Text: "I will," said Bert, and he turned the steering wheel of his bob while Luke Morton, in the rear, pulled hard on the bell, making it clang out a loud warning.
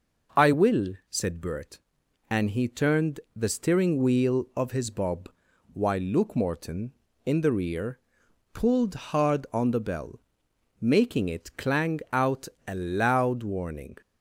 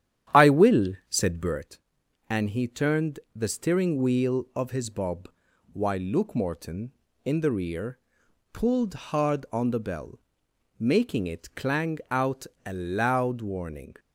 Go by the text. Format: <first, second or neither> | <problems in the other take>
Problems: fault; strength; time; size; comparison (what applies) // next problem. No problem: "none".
first | starts louder than the rest; strong; until 1.6 s; 10 dB // pauses between "bob" and "while"; at 5.2 s; 0.42 s long; also in the first // pauses between "out" and "a"; slight; at 12.4 s; 0.18 s long; slight in the first